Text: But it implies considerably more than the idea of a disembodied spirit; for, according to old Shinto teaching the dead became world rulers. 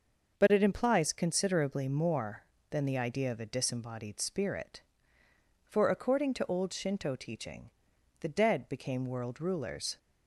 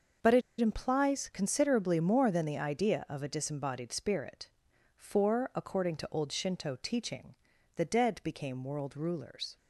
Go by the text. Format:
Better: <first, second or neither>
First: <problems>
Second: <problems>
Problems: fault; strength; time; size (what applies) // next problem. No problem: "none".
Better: first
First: starts louder than the rest; until 1.4 s; 6.5 dB // pauses between "teaching" and "the"; noticeable; at 7.6 s; 0.50 s long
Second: starts louder than the rest; noticeable; until 1.4 s; 6 dB // pauses between "it" and "implies"; slight; at 0.4 s; 0.19 s long // pauses between "teaching" and "the"; at 7.3 s; 0.40 s long